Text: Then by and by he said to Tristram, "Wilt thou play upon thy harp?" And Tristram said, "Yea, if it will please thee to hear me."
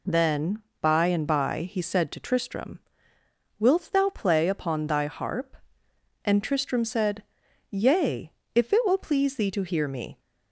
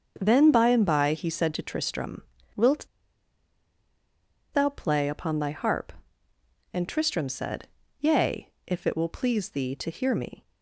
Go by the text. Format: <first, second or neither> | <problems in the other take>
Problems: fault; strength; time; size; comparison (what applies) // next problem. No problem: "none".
first | starts louder than the rest; until 1.1 s; 7 dB // pauses between "Wilt" and "thou"; strong; at 2.8 s; 1.6 s long